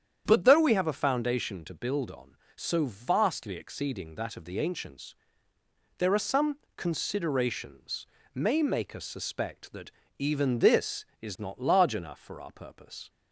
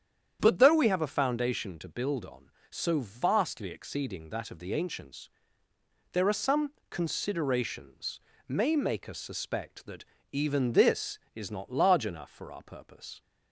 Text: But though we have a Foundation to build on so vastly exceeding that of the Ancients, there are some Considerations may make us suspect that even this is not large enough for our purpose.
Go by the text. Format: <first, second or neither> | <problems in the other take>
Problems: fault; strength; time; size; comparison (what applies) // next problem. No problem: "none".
neither | starts louder than the rest; strong; the same in both // pauses between "some" and "Considerations"; slight; the same in both // pauses between "Considerations" and "may"; slight; the same in both // pauses between "that" and "even"; slight; the same in both